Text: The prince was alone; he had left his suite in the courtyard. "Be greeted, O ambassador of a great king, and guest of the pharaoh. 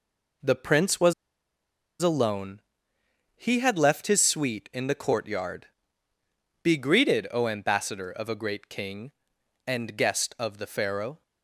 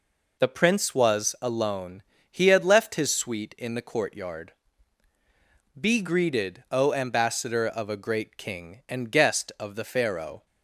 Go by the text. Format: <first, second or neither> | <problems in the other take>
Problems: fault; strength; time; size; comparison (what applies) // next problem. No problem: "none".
second | pauses between "was" and "alone"; noticeable; at 1.1 s; 0.88 s long